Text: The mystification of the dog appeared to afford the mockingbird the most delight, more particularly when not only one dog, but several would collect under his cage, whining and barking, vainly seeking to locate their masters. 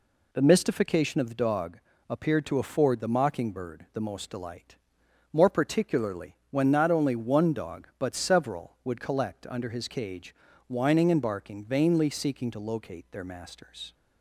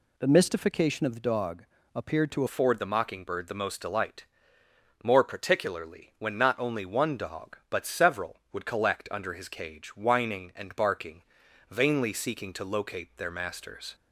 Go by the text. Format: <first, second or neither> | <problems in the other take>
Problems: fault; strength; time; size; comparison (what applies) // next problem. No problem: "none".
first | pauses between "dog" and "appeared"; slight; at 1.6 s; 0.30 s long; slight in the first // changes voice at "afford"; from 2.4 s on; 11.5 s long